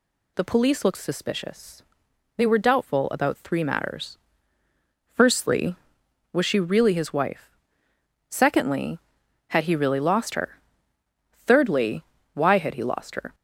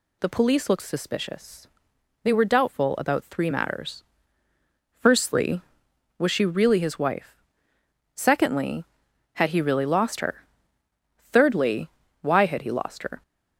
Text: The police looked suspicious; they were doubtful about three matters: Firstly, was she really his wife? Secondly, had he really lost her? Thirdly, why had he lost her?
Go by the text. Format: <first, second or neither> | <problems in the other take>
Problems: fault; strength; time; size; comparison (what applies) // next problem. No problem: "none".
neither | none